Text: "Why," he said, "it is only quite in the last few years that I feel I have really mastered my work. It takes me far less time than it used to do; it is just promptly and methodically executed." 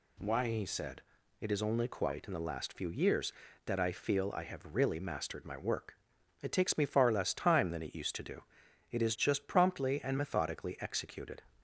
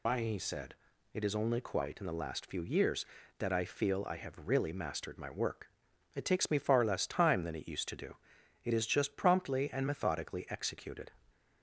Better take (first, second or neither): first